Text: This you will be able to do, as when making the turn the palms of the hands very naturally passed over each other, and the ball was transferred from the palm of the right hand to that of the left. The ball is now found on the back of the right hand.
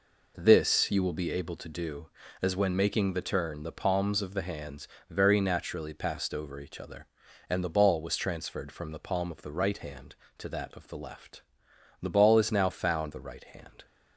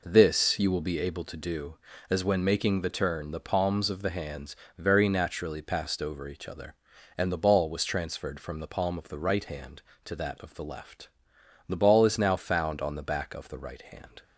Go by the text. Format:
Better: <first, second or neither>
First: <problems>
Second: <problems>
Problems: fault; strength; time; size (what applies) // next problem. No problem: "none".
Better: second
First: pauses between "hands" and "very"; slight; at 4.8 s; 0.20 s long // skips "on the back of"; at 13.1 s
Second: pauses between "hands" and "very"; slight; at 4.5 s; 0.20 s long